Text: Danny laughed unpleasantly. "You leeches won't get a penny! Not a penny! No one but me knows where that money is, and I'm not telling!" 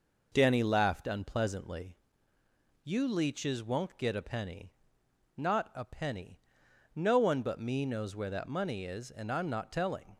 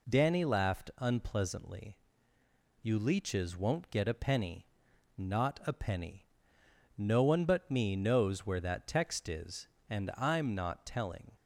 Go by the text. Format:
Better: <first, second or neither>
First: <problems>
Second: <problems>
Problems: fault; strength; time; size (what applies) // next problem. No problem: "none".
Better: first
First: none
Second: says "text" for "money"; at 8.8 s